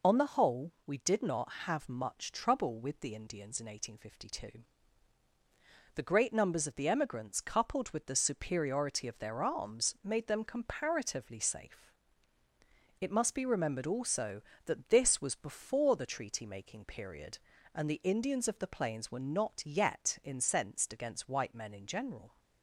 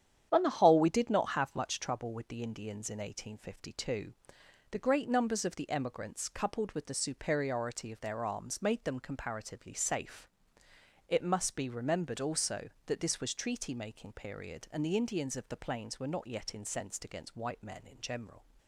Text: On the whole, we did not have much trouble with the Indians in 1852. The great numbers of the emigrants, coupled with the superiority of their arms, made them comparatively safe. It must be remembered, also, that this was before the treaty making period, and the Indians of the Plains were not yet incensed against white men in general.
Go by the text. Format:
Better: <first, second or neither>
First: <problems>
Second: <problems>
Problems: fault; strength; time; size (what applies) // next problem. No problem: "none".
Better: first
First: none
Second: starts louder than the rest; strong; until 1.3 s; 9 dB // skips "before the"; at 13.3 s